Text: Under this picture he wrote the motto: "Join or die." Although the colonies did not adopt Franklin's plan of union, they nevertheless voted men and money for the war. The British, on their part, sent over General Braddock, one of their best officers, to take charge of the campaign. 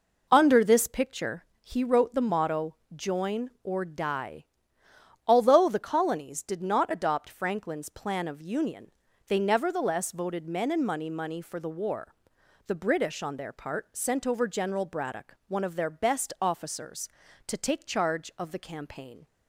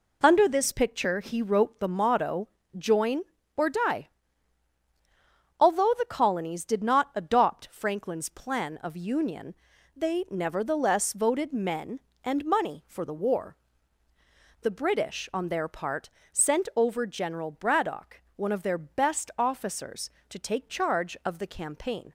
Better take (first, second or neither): second